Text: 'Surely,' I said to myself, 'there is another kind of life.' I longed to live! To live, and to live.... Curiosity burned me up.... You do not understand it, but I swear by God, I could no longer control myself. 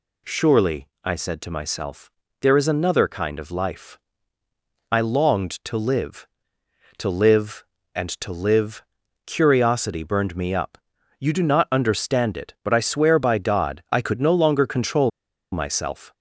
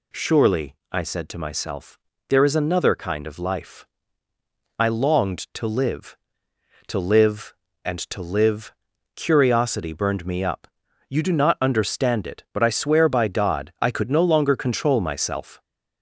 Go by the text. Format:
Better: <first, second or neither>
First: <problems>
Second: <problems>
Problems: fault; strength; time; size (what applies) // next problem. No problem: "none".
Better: second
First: pauses between "control" and "myself"; at 15.1 s; 0.42 s long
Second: none